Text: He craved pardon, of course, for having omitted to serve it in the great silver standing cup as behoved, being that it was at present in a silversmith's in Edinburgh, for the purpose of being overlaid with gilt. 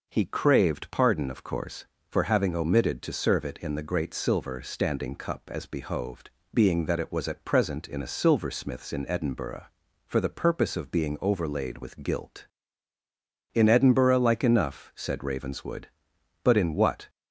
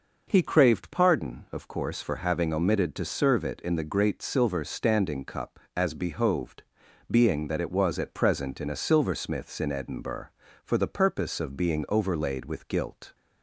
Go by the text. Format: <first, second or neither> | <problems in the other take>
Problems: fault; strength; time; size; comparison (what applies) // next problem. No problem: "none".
second | goes on to say "In Edinburgh like enough said Ravenswood but in what"; strong; from 13.5 s on; 3.5 s long